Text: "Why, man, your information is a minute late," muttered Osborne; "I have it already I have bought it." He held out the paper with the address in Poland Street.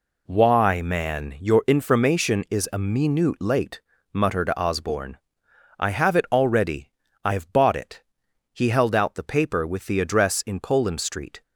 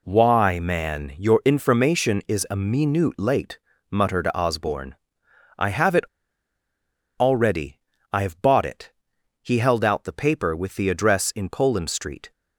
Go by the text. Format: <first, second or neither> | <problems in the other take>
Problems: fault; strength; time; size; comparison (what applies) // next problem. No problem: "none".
first | pauses between "it" and "already"; at 6.0 s; 1.1 s long // pauses between "already" and "I"; slight; at 7.7 s; 0.34 s long; slight in the first